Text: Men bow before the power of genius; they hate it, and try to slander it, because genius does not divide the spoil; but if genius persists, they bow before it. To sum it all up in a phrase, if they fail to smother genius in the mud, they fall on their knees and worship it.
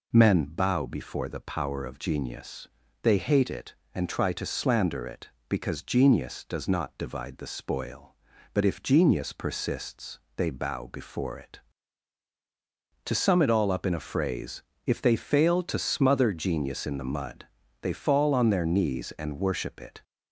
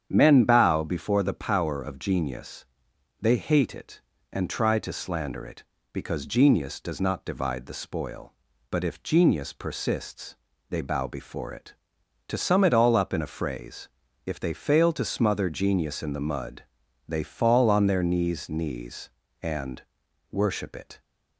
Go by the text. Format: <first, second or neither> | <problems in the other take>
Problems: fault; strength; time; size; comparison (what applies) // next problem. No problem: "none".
first | starts louder than the rest; strong; until 1.1 s; 8.5 dB // says "knees" twice; at 18.4 s // pauses between "and" and "worship"; noticeable; at 19.8 s; 0.48 s long